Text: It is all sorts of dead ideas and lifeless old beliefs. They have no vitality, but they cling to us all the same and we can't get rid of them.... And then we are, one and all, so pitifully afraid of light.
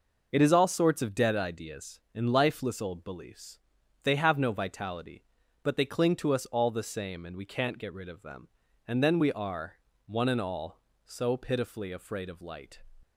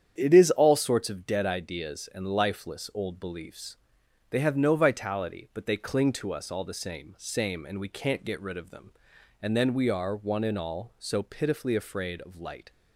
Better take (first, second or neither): first